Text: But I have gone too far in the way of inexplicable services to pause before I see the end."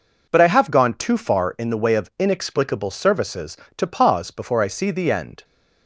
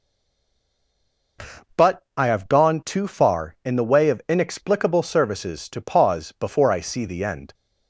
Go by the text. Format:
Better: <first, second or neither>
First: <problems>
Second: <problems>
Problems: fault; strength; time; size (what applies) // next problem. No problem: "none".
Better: first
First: none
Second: stays silent before the first word; noticeable; until 1.3 s; 1.3 s long // pauses between "But" and "I"; slight; at 2.0 s; 0.16 s long